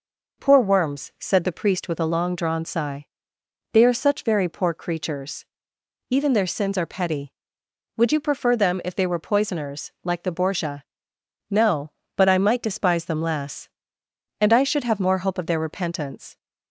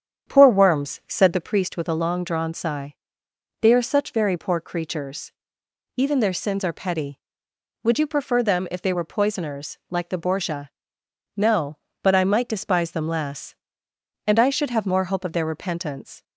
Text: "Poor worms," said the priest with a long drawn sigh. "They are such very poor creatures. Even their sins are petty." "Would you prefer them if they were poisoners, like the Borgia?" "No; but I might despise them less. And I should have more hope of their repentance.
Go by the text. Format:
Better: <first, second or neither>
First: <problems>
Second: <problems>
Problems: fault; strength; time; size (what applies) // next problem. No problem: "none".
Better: first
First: none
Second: starts louder than the rest; strong; until 1.4 s; 8.5 dB